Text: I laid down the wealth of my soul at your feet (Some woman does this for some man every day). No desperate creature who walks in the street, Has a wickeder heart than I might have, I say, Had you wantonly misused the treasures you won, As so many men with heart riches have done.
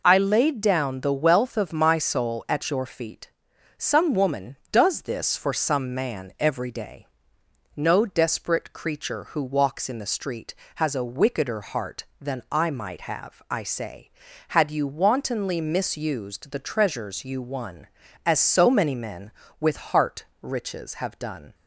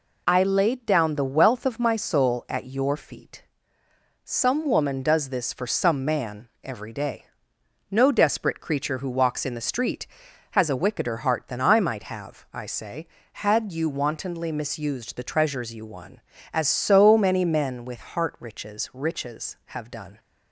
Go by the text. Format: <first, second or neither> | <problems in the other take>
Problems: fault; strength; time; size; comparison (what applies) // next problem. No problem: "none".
first | pauses between "man" and "every"; slight; at 6.4 s; 0.16 s long // says "riches" twice; at 18.9 s